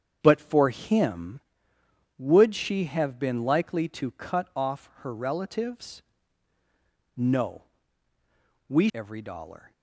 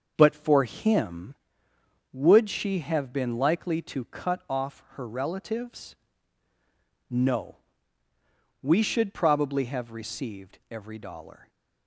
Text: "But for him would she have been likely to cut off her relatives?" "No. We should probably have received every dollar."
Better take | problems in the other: second | starts louder than the rest; strong; until 1.2 s; 8 dB; also in the second // skips "should probably have received"; at 8.9 s

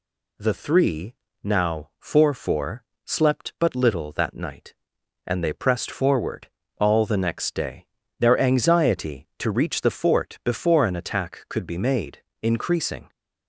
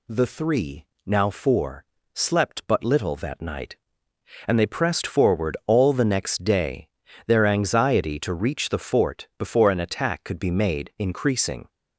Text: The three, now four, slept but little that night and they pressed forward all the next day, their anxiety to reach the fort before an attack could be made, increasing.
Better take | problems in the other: second | says "four" twice; at 2.3 s // pauses between "forward" and "all"; slight; at 6.4 s; 0.32 s long

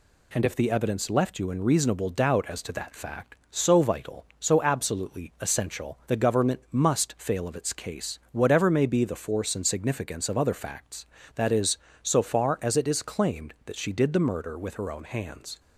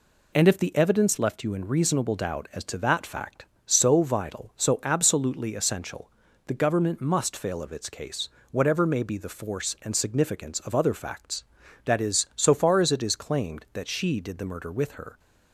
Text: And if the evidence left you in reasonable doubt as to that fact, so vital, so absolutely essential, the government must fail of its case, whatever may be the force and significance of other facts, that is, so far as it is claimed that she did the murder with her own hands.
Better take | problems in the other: first | stops before "own hands"; at 15.1 s

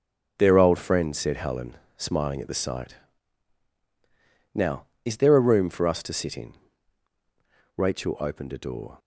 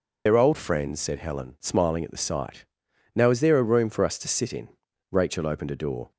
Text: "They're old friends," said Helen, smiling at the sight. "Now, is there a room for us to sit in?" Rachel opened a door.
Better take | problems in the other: first | loses the start of "They're"; at 0.2 s; 85 ms

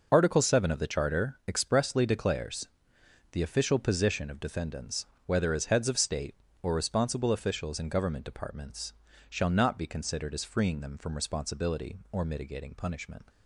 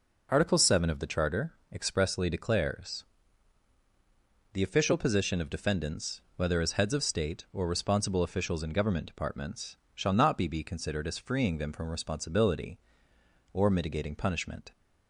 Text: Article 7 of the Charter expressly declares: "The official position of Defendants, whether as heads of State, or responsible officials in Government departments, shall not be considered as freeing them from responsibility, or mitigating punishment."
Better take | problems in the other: first | pauses between "Charter" and "expressly"; slight; at 1.5 s; 0.18 s long // says "be" twice; at 10.4 s

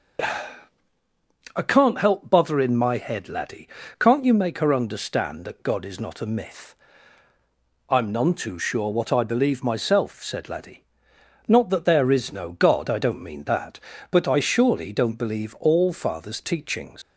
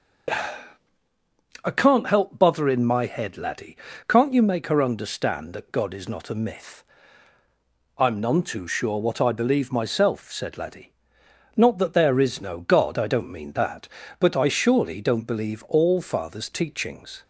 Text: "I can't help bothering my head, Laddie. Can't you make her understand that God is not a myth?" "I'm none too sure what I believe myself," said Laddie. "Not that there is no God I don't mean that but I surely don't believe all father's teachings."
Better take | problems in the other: second | leaves "teachings" unfinished; at 17.0 s; 125 ms

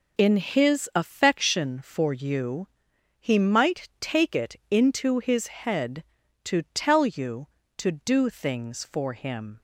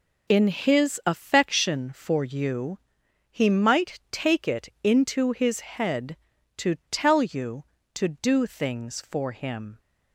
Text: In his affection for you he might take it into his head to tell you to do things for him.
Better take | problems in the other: neither | pauses between "you" and "he"; noticeable; the same in both // pauses between "it" and "into"; slight; the same in both

